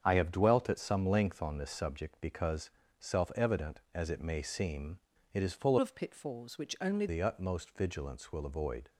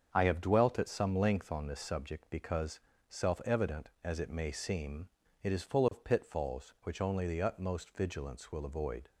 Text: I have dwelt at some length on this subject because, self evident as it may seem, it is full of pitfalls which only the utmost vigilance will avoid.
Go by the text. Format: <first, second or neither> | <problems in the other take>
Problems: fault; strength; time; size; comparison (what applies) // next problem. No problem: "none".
second | starts louder than the rest; strong; until 1.0 s; 8 dB; strong in the second // changes voice from "of" to "only"; from 5.7 to 7.0 s; 1.3 s long